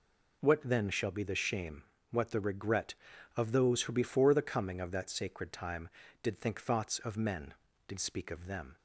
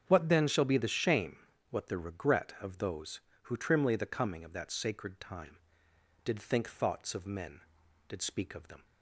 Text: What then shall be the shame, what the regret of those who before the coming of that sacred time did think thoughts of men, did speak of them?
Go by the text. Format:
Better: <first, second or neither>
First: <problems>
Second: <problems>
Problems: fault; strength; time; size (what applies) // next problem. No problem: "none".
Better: first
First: none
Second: starts louder than the rest; strong; until 1.0 s; 7.5 dB // says "trimly" for "before"; at 3.5 s